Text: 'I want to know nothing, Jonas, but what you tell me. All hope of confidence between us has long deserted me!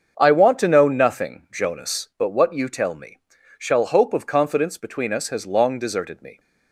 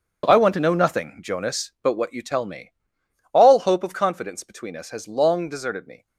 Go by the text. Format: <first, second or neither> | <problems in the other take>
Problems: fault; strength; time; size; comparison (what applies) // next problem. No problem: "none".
second | starts louder than the rest; until 1.2 s; 7 dB; also in the second // says "Shall" for "All"; at 3.5 s